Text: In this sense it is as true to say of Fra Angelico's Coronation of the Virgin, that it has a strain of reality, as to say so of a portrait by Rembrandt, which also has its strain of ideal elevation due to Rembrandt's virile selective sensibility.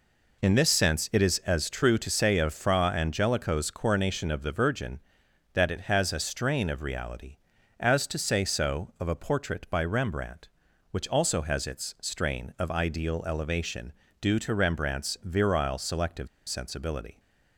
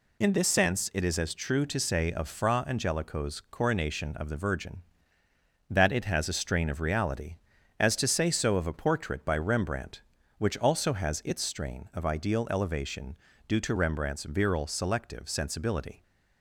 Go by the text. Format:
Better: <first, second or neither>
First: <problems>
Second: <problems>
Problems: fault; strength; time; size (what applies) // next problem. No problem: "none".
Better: second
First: pauses between "elevation" and "due"; slight; at 13.9 s; 0.28 s long // pauses between "selective" and "sensibility"; slight; at 16.2 s; 0.21 s long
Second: pauses between "elevation" and "due"; slight; at 13.1 s; 0.32 s long